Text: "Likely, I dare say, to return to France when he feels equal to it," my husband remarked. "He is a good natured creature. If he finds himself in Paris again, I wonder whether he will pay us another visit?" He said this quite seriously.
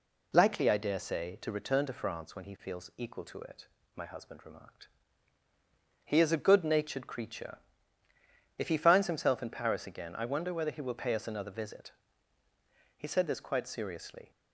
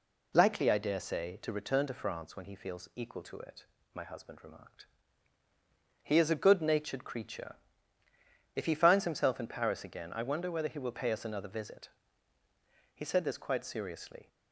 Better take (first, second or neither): neither